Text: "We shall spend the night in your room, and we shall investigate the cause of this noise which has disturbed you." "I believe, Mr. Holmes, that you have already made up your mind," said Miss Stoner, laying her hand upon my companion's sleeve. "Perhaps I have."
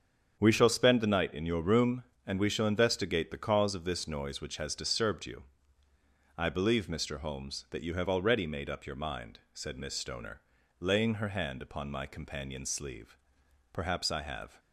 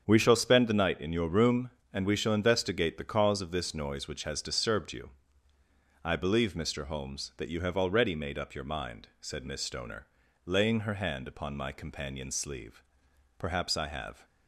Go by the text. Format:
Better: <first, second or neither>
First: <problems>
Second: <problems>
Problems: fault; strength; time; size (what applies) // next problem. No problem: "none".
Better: neither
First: starts louder than the rest; strong; until 1.3 s; 7.5 dB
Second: starts louder than the rest; strong; until 1.0 s; 7.5 dB